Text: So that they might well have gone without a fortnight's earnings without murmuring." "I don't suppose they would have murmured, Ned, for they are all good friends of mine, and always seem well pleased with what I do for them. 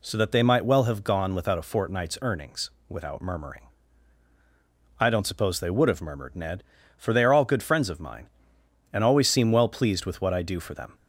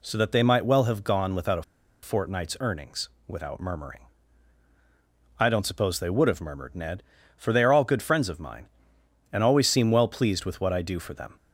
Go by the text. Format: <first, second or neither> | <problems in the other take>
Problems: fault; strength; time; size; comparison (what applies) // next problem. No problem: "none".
first | pauses between "a" and "fortnight's"; at 1.6 s; 0.41 s long // pauses between "earnings" and "without"; slight; at 3.0 s; 0.18 s long; slight in the first